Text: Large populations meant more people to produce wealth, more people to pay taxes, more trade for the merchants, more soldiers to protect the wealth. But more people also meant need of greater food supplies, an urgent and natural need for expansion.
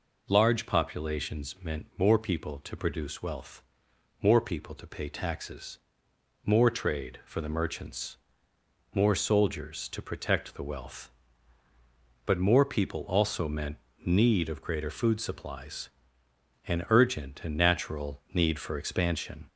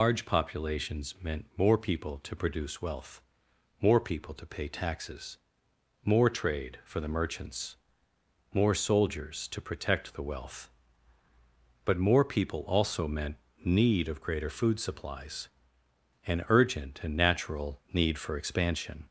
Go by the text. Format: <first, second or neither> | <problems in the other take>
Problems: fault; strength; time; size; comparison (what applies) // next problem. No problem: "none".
first | loses the start of "Large"; at 0.0 s; 130 ms // pauses between "meant" and "need"; slight; at 13.3 s; 0.26 s long; slight in the first